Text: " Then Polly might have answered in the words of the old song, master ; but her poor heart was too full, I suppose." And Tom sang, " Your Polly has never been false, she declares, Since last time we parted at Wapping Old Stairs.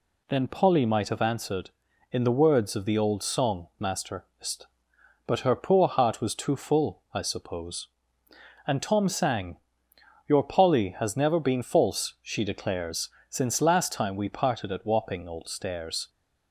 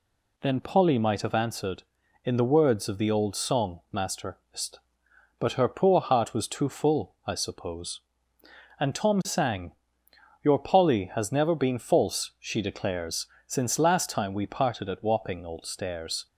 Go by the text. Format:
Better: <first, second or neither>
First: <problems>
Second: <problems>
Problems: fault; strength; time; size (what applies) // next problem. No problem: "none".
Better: neither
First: none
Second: none